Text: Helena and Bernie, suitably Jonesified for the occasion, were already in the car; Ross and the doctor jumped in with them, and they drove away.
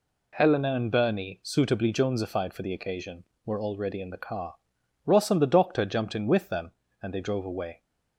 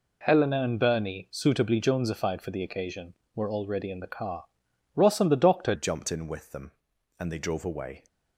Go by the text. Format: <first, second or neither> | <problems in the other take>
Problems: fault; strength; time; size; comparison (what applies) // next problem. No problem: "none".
first | changes voice at "jumped"; from 5.7 s on; 2.3 s long